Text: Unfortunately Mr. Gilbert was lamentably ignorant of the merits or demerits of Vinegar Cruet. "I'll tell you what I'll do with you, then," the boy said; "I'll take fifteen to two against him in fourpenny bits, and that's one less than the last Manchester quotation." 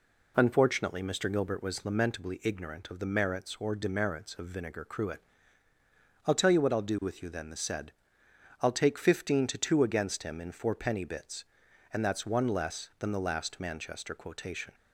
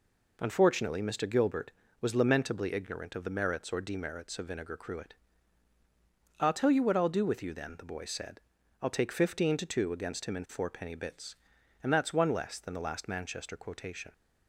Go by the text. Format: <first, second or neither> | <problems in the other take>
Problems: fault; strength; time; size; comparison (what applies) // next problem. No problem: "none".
second | skips "boy"; at 7.5 s